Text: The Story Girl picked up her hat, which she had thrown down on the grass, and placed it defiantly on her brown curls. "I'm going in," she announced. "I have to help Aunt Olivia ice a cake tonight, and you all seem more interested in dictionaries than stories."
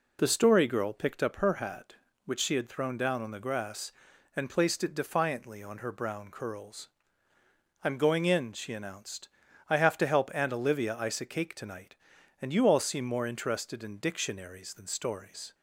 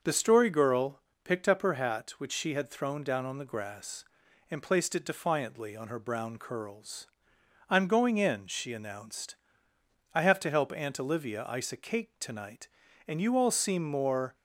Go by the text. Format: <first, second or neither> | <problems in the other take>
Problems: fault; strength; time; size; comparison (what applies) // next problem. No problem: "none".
first | starts louder than the rest; until 1.0 s; 6.5 dB // pauses between "Girl" and "picked"; slight; at 1.0 s; 0.22 s long // stops before "interested in dictionaries than stories"; at 14.3 s